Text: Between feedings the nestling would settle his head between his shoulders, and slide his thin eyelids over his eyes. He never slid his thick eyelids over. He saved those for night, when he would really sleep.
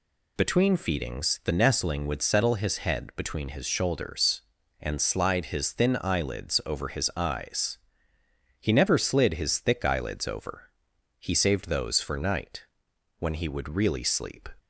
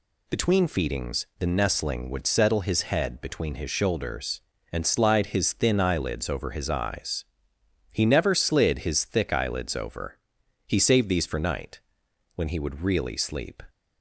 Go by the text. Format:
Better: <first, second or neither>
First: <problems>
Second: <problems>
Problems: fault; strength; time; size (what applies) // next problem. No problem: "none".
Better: first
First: none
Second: says "these" for "those"; at 11.0 s